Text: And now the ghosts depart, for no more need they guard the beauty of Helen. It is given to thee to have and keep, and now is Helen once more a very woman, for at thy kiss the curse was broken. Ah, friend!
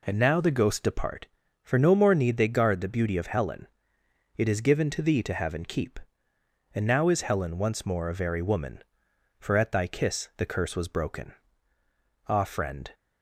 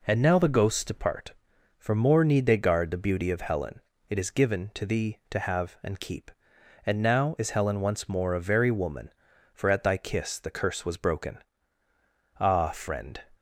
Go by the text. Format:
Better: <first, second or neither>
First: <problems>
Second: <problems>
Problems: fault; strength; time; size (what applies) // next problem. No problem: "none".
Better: first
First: none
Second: skips "no"; at 1.9 s